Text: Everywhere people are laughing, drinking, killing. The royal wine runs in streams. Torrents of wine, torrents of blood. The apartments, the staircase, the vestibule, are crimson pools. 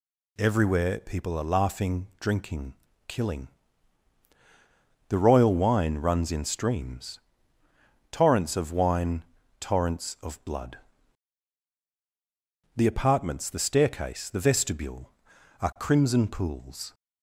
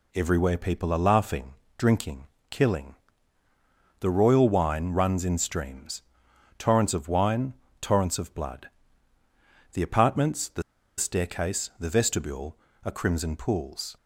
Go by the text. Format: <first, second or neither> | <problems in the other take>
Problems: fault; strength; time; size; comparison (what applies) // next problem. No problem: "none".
first | pauses between "the" and "staircase"; slight; at 10.6 s; 0.35 s long